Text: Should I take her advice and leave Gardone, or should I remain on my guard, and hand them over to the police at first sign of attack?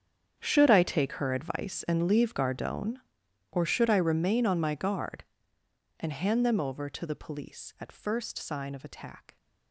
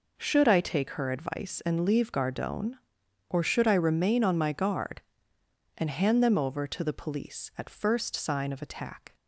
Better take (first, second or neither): second